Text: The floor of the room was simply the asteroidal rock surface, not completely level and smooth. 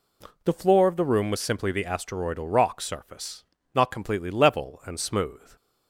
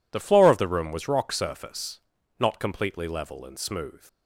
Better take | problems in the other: first | skips "simply the asteroidal"; at 1.0 s

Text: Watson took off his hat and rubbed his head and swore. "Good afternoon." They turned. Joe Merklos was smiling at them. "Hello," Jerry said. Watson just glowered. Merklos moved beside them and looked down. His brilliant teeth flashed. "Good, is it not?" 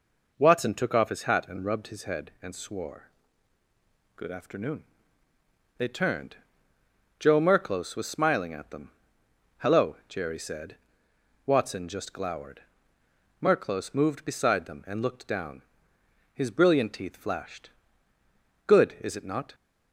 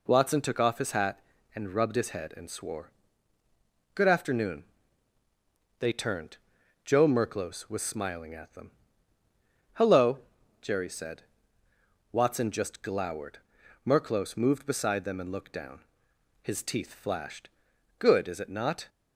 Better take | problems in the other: first | skips "brilliant"; at 16.6 s

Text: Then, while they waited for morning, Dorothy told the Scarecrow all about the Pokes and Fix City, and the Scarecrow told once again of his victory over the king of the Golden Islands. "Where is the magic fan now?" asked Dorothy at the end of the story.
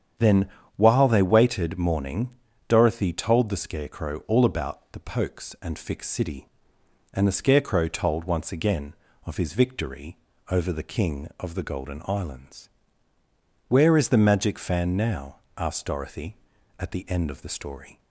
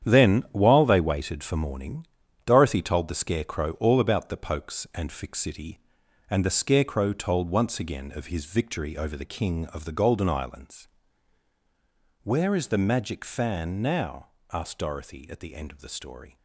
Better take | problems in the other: second | starts louder than the rest; strong; until 1.5 s; 8.5 dB; strong in the second // skips "for"; at 1.7 s // pauses between "victory" and "over"; slight; at 10.1 s; 0.32 s long

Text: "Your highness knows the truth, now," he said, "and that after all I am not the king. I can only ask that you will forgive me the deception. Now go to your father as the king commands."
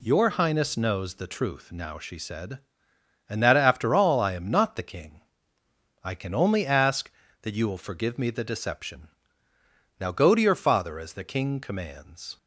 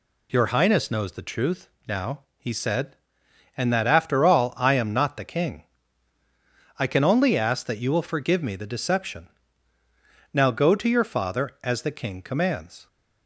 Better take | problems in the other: second | says "she" for "he"; at 1.9 s

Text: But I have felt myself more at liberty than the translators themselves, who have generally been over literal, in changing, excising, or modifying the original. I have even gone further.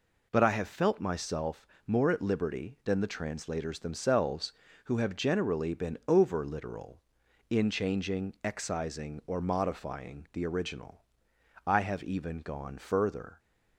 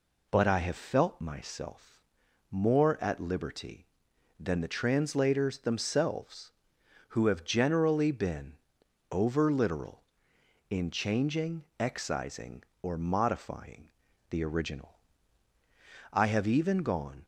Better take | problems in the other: first | pauses between "myself" and "more"; noticeable; at 1.9 s; 0.52 s long; slight in the first // pauses between "been" and "over"; noticeable; at 8.5 s; 0.56 s long // pauses between "modifying" and "the"; at 13.8 s; 0.40 s long // stops before "further"; at 17.2 s

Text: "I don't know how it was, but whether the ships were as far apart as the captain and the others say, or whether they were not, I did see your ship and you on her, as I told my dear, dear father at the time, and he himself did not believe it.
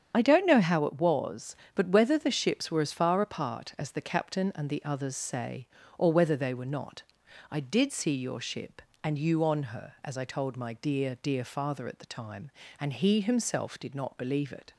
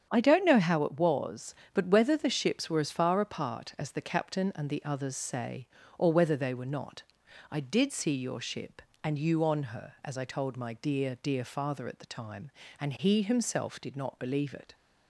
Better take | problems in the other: second | loses the start of "I"; at 0.1 s; 30 ms // starts louder than the rest; strong; until 1.1 s; 8.5 dB; strong in the second

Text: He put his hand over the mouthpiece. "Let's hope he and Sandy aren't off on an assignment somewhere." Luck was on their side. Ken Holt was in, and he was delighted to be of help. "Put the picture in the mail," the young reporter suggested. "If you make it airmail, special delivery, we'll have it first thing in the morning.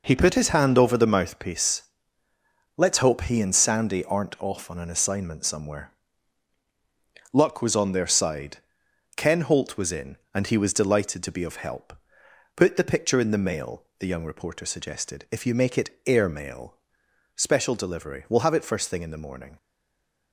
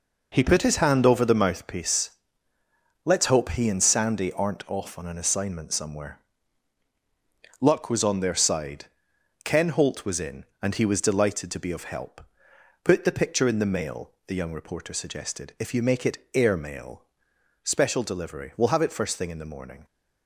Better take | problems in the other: second | stays silent after the last word; slight; from 19.5 s on; 0.8 s long

